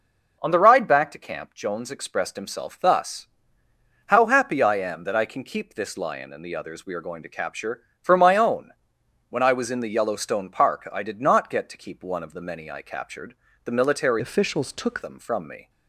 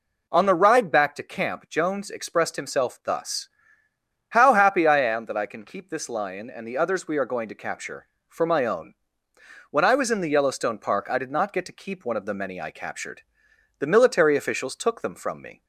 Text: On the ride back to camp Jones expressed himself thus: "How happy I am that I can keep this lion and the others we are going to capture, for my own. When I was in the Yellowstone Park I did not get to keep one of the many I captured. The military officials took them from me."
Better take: second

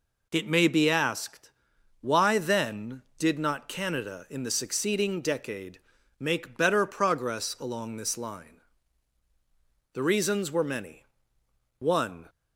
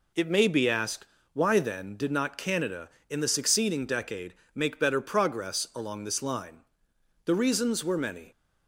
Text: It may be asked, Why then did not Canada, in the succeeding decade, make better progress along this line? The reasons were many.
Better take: second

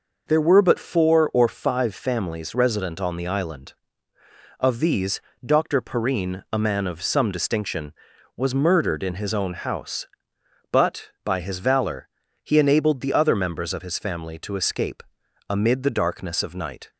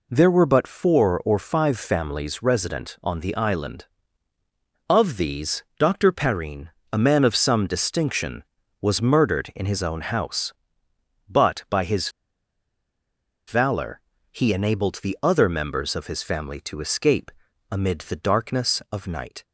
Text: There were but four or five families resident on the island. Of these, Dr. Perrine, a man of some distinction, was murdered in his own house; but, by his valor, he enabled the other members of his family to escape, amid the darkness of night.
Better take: first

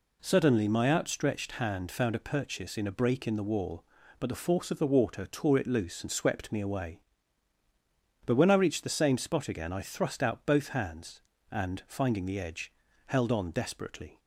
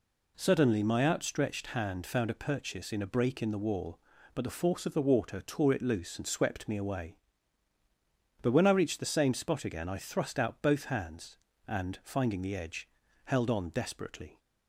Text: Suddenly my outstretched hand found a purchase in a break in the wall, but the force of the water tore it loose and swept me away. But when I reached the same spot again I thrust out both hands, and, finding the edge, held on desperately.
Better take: neither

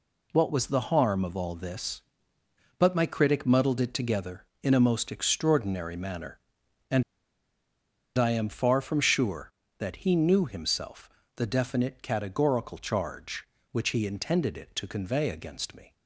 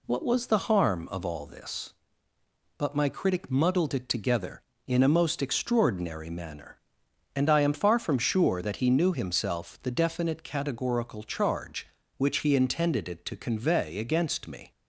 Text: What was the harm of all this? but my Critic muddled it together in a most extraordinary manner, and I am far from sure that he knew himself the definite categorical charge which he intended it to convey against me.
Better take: second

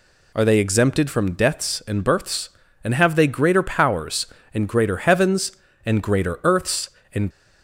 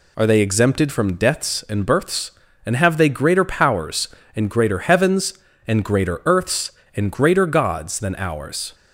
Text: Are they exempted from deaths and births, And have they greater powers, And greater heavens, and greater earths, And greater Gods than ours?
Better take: second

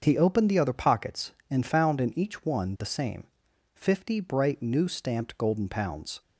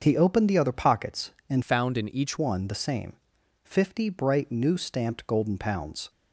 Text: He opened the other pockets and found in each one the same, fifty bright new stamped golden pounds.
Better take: first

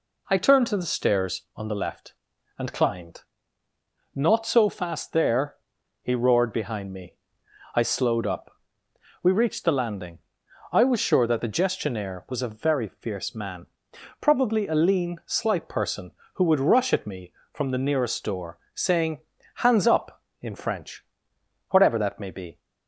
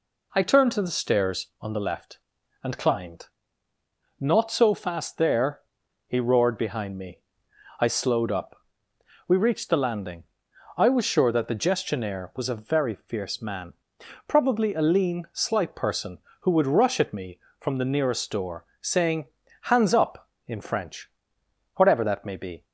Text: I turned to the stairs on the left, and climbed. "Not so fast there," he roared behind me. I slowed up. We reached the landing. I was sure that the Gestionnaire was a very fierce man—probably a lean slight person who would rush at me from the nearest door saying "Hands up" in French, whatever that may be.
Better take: neither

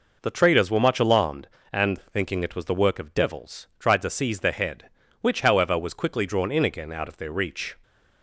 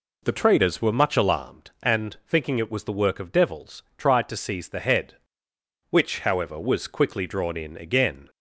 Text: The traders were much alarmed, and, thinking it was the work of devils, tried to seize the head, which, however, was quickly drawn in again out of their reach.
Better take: first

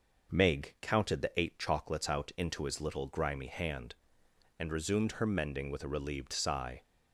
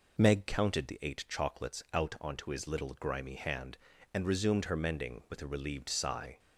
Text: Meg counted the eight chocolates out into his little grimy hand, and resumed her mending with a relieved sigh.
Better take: first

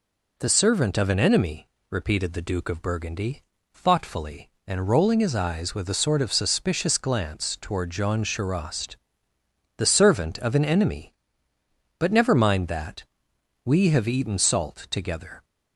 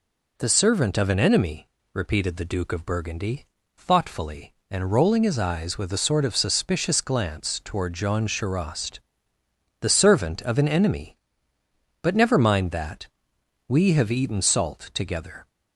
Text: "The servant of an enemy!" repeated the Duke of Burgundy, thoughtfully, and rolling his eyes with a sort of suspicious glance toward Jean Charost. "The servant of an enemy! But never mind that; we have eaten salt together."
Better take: neither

